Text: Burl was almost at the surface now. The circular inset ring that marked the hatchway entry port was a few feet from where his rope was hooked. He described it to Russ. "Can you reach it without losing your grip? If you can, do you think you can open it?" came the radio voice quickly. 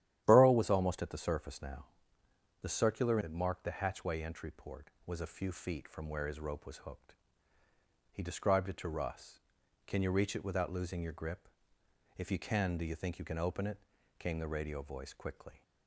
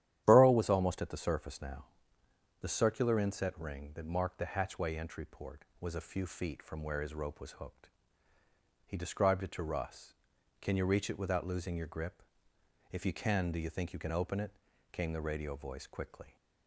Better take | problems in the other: second | starts louder than the rest; strong; until 1.2 s; 11.5 dB; strong in the second // skips "inset ring"; at 3.1 s

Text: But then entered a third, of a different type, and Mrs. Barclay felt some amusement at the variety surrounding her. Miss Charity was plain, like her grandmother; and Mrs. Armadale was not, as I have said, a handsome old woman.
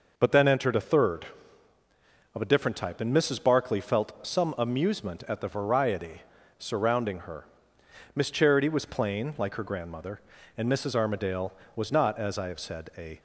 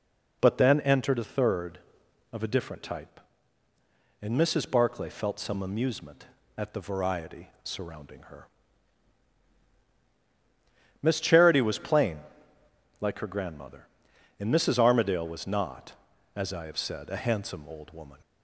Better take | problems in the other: second | pauses between "variety" and "surrounding"; slight; at 6.2 s; 0.36 s long; slight in the second // stops before "handsome old woman"; at 13.1 s

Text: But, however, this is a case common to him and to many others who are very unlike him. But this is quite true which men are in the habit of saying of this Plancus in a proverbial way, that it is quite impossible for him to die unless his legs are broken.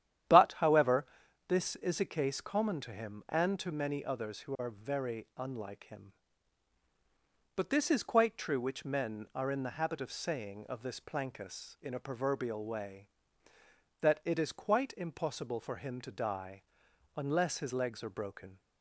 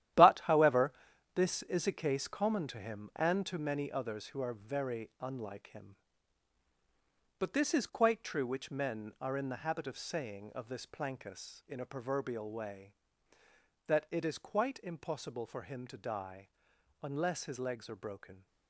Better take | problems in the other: first | gets quieter; strong; throughout; 9.5 dB // starts louder than the rest; strong; until 1.5 s; 12 dB; strong in the first // pauses between "die" and "unless"; noticeable; at 16.4 s; 0.54 s long; noticeable in the first

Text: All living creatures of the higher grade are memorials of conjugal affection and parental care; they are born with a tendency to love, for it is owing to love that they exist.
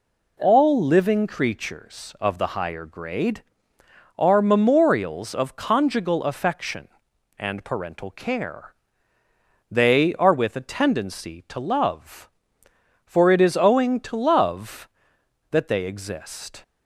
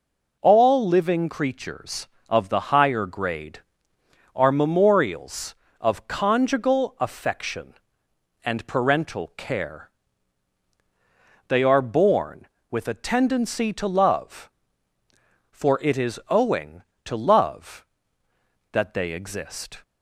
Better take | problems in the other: second | skips "born"; at 10.3 s

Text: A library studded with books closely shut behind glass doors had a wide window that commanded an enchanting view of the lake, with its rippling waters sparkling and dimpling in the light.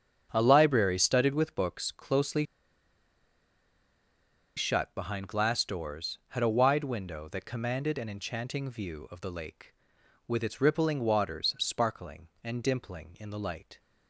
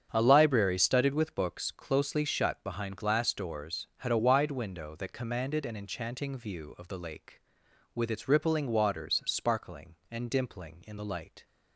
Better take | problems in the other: second | starts louder than the rest; strong; until 1.3 s; 8 dB; strong in the second // pauses between "closely" and "shut"; strong; at 2.4 s; 2.1 s long

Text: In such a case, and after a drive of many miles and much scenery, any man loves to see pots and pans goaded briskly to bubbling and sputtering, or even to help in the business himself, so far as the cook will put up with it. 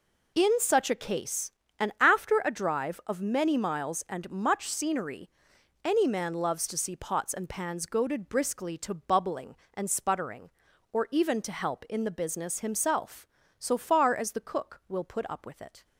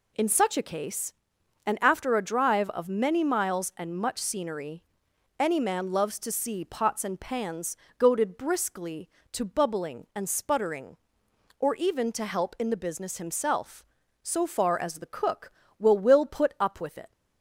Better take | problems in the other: first | pauses between "pans" and "goaded"; slight; at 7.7 s; 0.24 s long // says "will" twice; at 15.9 s

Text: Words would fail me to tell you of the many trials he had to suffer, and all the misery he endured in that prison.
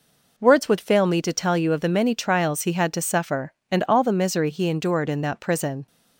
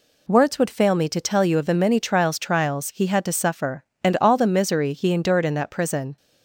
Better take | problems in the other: first | says "trials" twice; at 2.3 s

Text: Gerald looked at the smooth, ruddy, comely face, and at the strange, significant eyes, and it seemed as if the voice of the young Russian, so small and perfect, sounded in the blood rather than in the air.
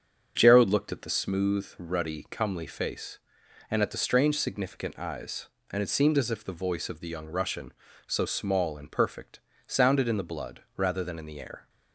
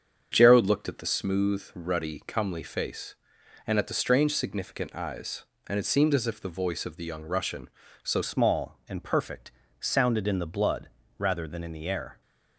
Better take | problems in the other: first | starts louder than the rest; strong; until 1.3 s; 7.5 dB; also in the first // changes voice at "small"; from 8.2 s on; 4.0 s long // pauses between "blood" and "rather"; slight; at 10.8 s; 0.28 s long

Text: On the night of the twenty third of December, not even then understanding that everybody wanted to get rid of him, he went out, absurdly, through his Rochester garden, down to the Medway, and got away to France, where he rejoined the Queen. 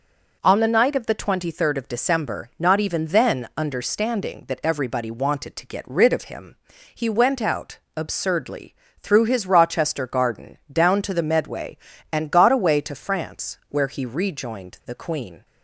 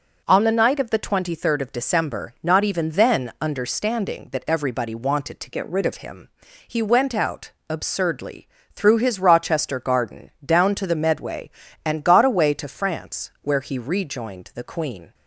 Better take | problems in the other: first | changes voice from "get" to "rid"; from 5.5 to 5.8 s; 0.3 s long

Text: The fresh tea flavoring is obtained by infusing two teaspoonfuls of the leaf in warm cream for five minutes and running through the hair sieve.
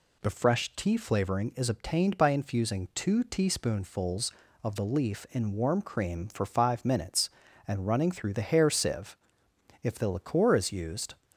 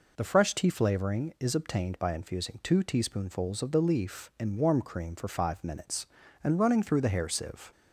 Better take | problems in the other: second | goes on to say "If the liqueur is used"; from 9.8 s on; 1.3 s long

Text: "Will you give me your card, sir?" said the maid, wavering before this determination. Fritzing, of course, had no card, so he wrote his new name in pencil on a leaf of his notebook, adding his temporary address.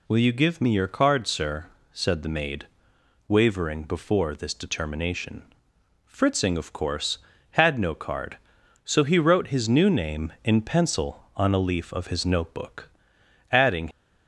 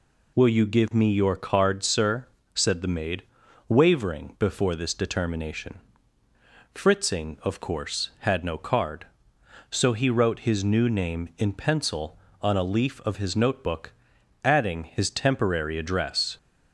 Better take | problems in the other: second | stops before "his temporary address"; at 13.9 s

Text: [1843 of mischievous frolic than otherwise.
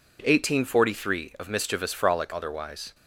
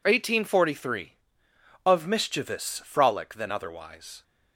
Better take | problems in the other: second | skips "than"; at 2.3 s

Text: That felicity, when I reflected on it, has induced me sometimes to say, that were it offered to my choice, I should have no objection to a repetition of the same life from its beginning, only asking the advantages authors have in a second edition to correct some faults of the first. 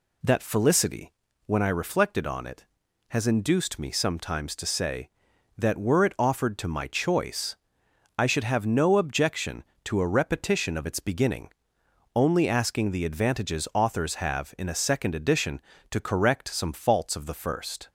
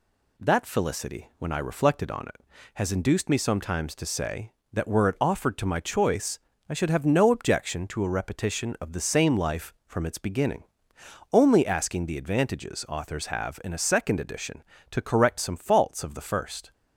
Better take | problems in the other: second | skips "the same life from"; at 10.8 s

